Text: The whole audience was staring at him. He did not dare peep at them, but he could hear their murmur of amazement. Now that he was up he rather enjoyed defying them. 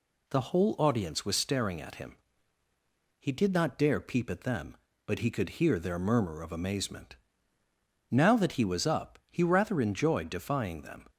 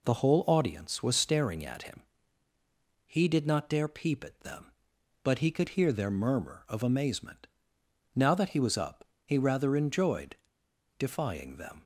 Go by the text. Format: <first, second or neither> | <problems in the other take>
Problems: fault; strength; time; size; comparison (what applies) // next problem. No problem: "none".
first | pauses between "up" and "he"; slight; at 9.0 s; 0.20 s long // pauses between "enjoyed" and "defying"; noticeable; at 10.3 s; 0.61 s long